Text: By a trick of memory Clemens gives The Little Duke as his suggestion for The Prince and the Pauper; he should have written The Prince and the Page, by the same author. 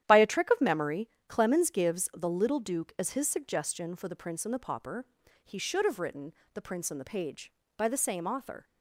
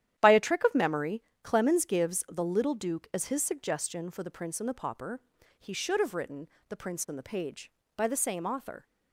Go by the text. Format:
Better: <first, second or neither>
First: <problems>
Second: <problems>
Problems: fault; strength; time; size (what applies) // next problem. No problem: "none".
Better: neither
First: starts louder than the rest; strong; until 1.0 s; 10.5 dB // pauses between "memory" and "Clemens"; slight; at 1.0 s; 0.20 s long // pauses between "written" and "The"; slight; at 6.3 s; 0.22 s long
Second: starts louder than the rest; strong; until 1.2 s; 10.5 dB // pauses between "memory" and "Clemens"; slight; at 1.2 s; 0.22 s long // pauses between "written" and "The"; slight; at 6.4 s; 0.22 s long